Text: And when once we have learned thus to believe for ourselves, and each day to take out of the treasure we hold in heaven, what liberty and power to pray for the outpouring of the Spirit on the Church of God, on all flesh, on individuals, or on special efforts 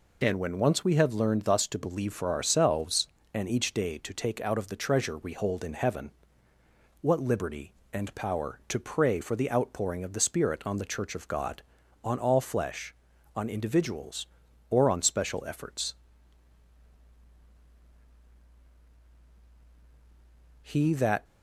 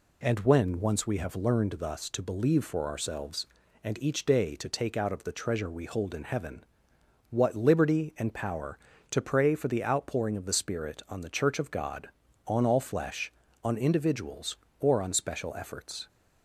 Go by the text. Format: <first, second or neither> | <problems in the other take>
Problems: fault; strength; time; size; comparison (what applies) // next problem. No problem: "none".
second | goes on to say "He that"; noticeable; from 20.6 s on; 0.62 s long